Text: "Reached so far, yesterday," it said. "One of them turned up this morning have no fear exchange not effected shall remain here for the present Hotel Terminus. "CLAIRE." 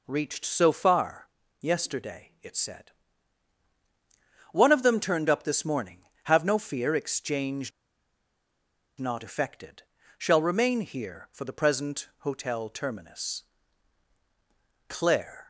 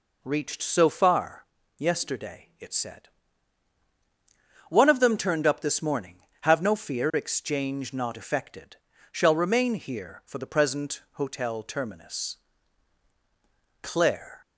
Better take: second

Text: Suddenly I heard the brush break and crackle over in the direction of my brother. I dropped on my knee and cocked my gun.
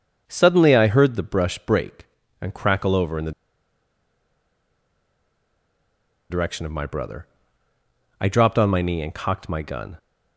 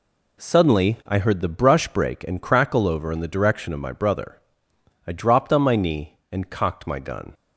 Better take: second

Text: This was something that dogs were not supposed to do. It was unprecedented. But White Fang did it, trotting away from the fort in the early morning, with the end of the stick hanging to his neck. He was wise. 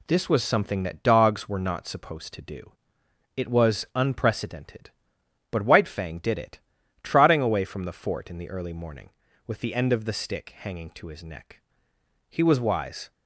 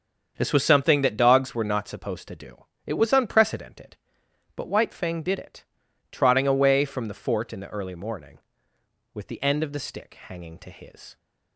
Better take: first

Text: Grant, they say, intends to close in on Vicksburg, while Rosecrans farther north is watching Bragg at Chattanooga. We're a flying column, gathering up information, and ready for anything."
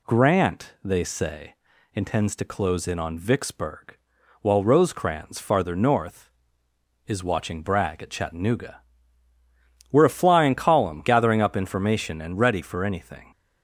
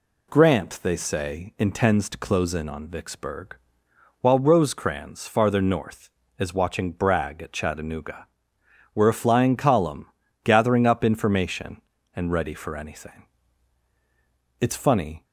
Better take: first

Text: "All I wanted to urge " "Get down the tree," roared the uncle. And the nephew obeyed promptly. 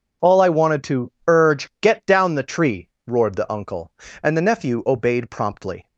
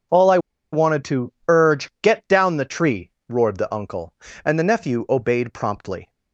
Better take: first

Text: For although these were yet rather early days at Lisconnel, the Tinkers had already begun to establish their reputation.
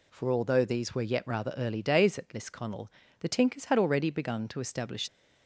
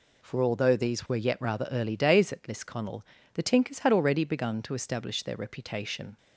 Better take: second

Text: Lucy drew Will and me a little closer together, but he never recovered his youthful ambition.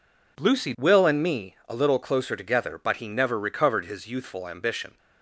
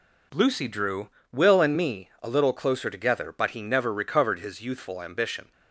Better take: second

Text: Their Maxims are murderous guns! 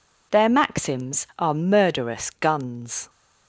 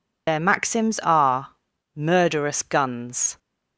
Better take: first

